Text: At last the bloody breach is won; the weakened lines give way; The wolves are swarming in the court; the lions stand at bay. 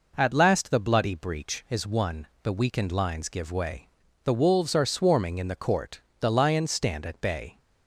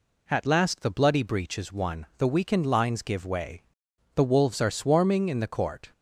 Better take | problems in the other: first | stops before "the lions stand at bay"; at 5.9 s

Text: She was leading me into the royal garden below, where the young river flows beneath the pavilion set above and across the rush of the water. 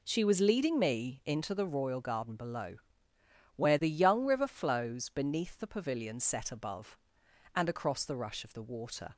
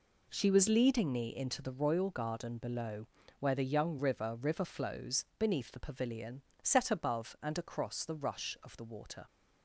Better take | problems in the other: first | says "river" twice; at 4.3 s // pauses between "pavilion" and "set"; slight; at 6.4 s; 0.20 s long

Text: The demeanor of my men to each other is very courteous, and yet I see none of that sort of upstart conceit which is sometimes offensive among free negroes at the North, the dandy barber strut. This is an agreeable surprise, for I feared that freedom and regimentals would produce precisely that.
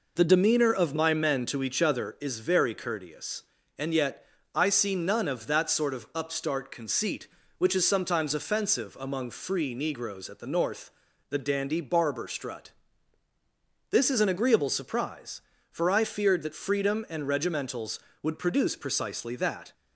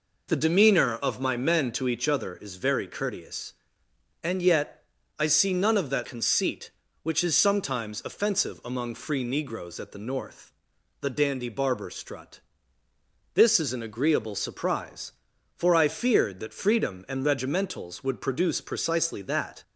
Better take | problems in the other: first | pauses between "yet" and "I"; slight; at 4.8 s; 0.34 s long; slight in the first // skips "sort of upstart"; at 6.0 s

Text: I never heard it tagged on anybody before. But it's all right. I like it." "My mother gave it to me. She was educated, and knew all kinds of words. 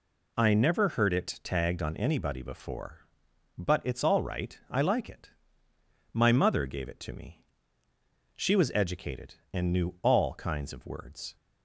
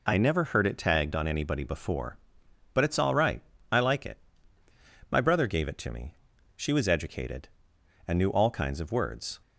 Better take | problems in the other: first | says "brother" for "mother"; at 5.1 s

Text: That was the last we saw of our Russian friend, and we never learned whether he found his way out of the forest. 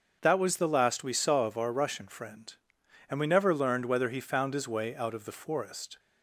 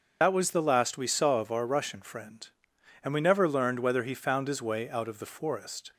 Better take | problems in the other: first | loses the start of "That"; at 0.2 s; 60 ms // starts louder than the rest; until 1.2 s; 6.5 dB; also in the first

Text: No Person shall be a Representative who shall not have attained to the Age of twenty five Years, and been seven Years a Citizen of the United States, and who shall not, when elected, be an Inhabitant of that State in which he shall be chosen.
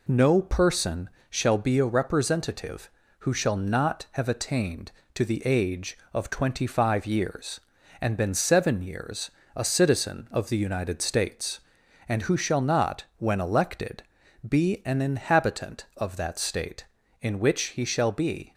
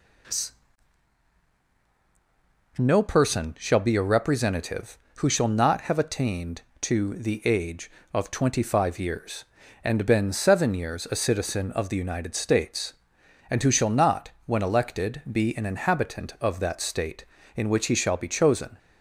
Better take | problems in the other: second | pauses between "Person" and "shall"; slight; at 1.0 s; 0.20 s long // pauses between "Years" and "a"; slight; at 9.2 s; 0.24 s long // stops before "chosen"; at 18.5 s

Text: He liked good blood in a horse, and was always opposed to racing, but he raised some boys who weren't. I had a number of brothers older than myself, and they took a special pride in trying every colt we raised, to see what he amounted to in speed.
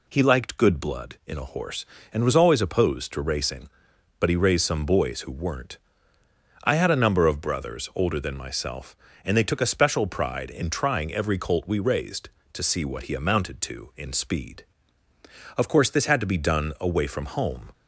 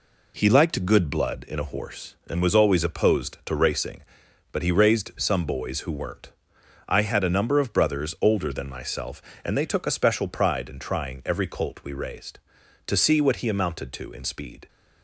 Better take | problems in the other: second | goes on to say "Of course this had to be done away from home"; strong; from 15.5 s on; 2.1 s long

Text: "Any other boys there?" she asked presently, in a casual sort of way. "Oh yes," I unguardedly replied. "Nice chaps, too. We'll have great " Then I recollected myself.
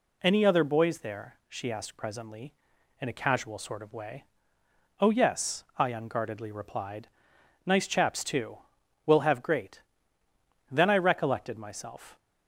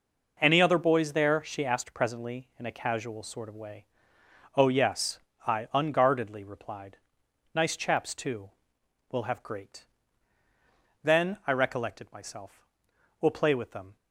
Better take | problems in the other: first | goes on to say "We'll play with them"; noticeable; from 13.2 s on; 0.76 s long

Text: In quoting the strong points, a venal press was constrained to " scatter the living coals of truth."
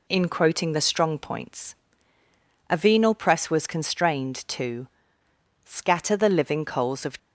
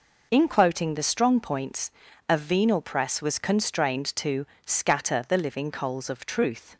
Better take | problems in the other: second | stops before "truth"; at 7.1 s

